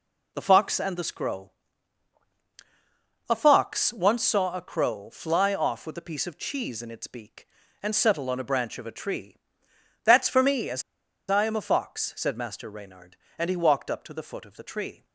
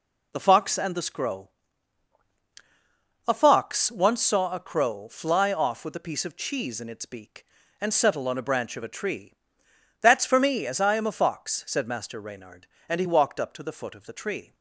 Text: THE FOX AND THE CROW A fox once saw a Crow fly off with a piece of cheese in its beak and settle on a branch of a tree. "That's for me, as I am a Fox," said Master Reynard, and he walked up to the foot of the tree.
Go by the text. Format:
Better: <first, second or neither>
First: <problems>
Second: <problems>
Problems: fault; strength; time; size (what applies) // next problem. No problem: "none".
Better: second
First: pauses between "CROW" and "A"; strong; at 1.5 s; 1.8 s long // pauses between "as" and "I"; noticeable; at 10.8 s; 0.46 s long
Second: pauses between "CROW" and "A"; strong; at 1.4 s; 1.8 s long